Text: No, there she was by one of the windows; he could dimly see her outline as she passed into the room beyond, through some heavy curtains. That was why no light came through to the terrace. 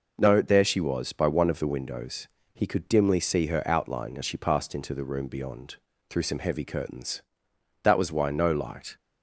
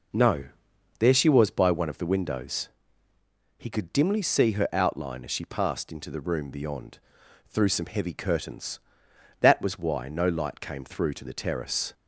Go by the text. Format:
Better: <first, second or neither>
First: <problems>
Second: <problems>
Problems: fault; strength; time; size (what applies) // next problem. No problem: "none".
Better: second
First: stops before "came through to the terrace"; at 8.9 s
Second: none